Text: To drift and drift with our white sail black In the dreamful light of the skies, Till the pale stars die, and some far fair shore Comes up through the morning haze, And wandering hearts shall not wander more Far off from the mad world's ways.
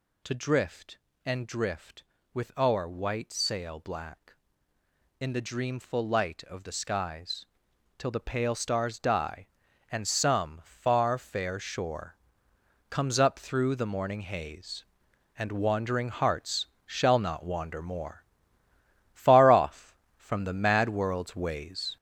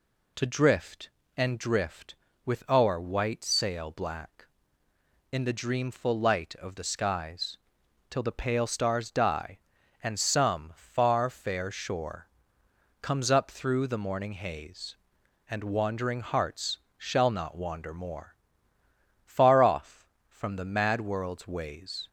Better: second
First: gets louder; throughout; 6.5 dB // pauses between "shore" and "Comes"; noticeable; at 12.1 s; 0.74 s long // pauses between "hearts" and "shall"; slight; at 16.6 s; 0.18 s long // pauses between "more" and "Far"; noticeable; at 18.2 s; 0.92 s long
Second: pauses between "shore" and "Comes"; noticeable; at 12.2 s; 0.74 s long // pauses between "hearts" and "shall"; slight; at 16.7 s; 0.18 s long // pauses between "more" and "Far"; noticeable; at 18.3 s; 0.92 s long

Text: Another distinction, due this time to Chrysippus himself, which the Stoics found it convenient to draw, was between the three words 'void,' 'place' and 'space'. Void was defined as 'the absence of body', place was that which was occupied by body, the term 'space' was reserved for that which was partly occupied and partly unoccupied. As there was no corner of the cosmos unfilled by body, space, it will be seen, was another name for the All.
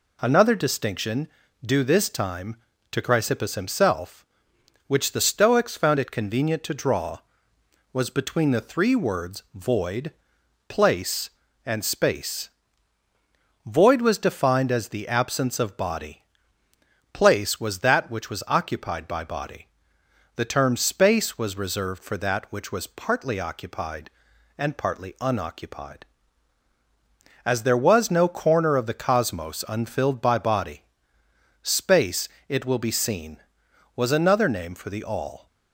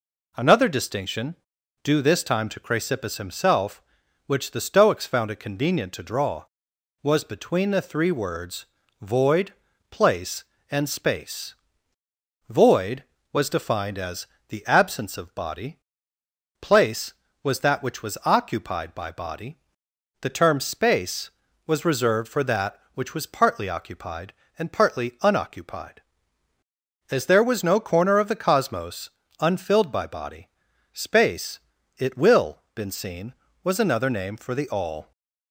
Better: first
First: none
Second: pauses between "words" and "void"; slight; at 8.6 s; 0.36 s long // pauses between "as" and "the"; slight; at 14.2 s; 0.22 s long // pauses between "cosmos" and "unfilled"; slight; at 29.0 s; 0.30 s long // says "been" for "be"; at 32.7 s

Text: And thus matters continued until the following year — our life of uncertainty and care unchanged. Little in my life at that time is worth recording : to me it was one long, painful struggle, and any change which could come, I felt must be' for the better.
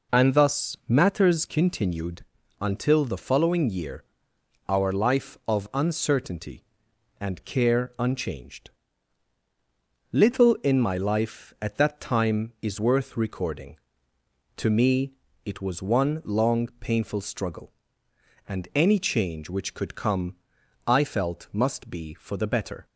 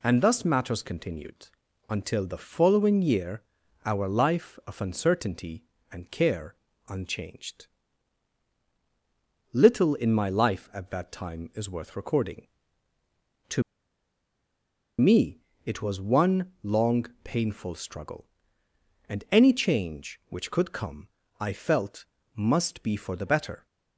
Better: first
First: pauses between "continued" and "until"; at 2.2 s; 0.38 s long // pauses between "me" and "it"; slight; at 15.1 s; 0.32 s long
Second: pauses between "continued" and "until"; at 1.4 s; 0.42 s long // pauses between "care" and "unchanged"; slight; at 6.5 s; 0.32 s long // pauses between "to" and "me"; strong; at 13.6 s; 1.3 s long // pauses between "me" and "it"; slight; at 15.3 s; 0.26 s long // pauses between "felt" and "must"; slight; at 22.0 s; 0.28 s long

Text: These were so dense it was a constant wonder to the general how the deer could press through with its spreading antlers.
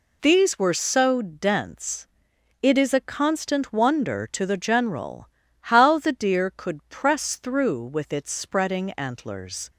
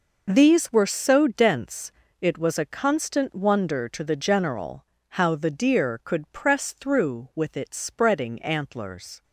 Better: second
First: pauses between "dense" and "it"; noticeable; at 2.0 s; 0.56 s long // says "is" for "was"; at 2.7 s // pauses between "general" and "how"; slight; at 5.2 s; 0.32 s long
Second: pauses between "dense" and "it"; slight; at 1.9 s; 0.30 s long // pauses between "general" and "how"; slight; at 4.8 s; 0.32 s long

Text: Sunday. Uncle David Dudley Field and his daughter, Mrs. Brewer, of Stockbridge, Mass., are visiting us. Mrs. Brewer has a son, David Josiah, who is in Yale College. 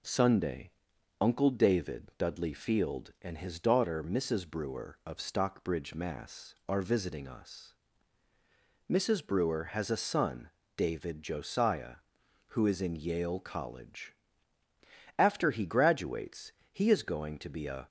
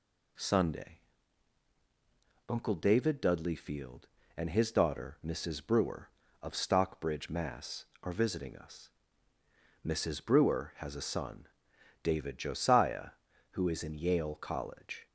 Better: second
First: goes on to say "After he graduates he is going to be a"; strong; from 15.1 s on; 2.7 s long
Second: none

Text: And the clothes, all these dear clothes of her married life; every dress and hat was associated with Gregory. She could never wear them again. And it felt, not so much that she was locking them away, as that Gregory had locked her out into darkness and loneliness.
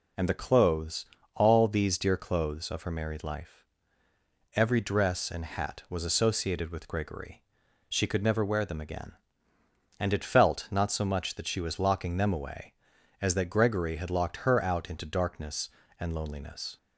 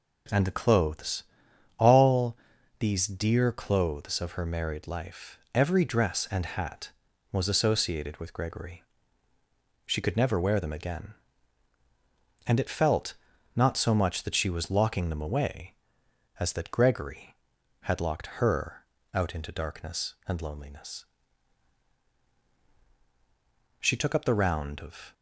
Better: first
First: none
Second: pauses between "all" and "these"; at 2.3 s; 0.42 s long // pauses between "her" and "out"; slight; at 18.8 s; 0.30 s long // goes on to say "She took up the round of"; from 23.7 s on; 1.3 s long

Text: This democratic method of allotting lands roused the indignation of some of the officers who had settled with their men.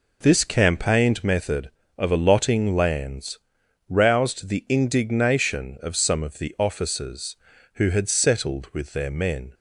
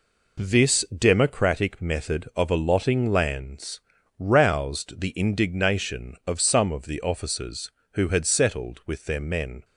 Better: second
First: says "campaigned" for "democratic"; at 0.4 s // pauses between "lands" and "roused"; noticeable; at 3.3 s; 0.50 s long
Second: pauses between "lands" and "roused"; at 3.8 s; 0.40 s long

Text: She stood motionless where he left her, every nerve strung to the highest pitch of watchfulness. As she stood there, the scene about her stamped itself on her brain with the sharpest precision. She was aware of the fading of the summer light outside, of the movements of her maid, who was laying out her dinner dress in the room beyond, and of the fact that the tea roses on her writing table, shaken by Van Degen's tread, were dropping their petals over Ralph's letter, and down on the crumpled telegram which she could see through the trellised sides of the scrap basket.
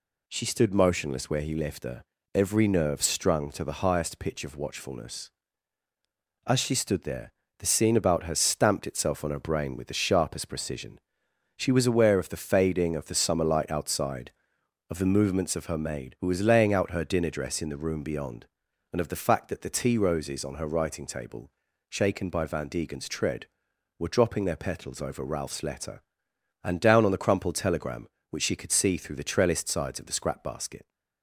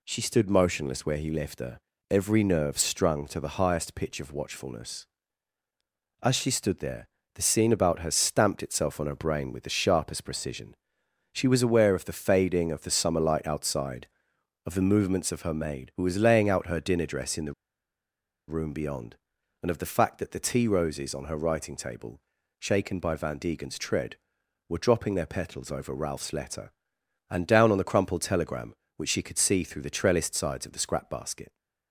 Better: first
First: none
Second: pauses between "the" and "room"; noticeable; at 17.5 s; 0.94 s long

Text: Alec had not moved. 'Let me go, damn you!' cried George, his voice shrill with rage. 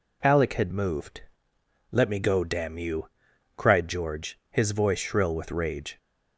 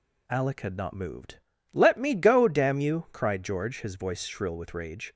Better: second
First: skips "not"; at 0.6 s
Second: none

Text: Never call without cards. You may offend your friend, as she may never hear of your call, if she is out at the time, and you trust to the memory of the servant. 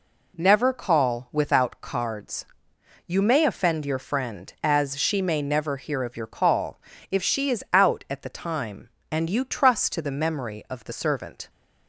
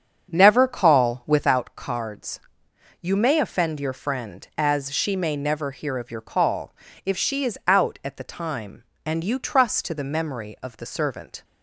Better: first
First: none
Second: starts louder than the rest; strong; until 1.5 s; 7.5 dB

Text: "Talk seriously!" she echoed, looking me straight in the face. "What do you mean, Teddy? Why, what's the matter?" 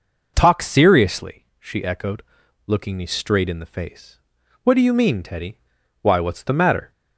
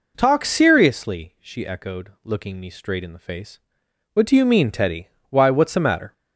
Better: neither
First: none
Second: none

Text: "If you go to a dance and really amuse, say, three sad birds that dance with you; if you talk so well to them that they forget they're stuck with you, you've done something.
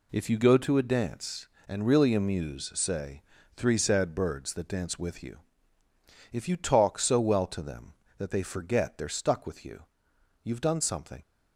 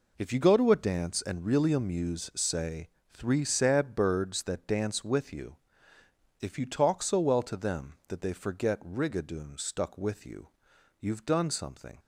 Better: first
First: none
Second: says "rigadoon" for "they're"; at 8.8 s

